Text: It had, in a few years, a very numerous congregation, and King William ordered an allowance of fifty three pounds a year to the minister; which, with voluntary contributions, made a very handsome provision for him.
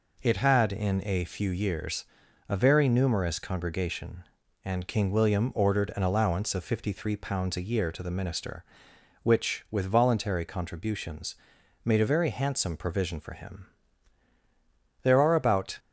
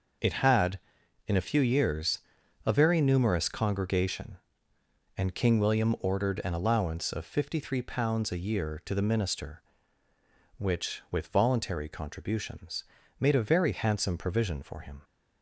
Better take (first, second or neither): second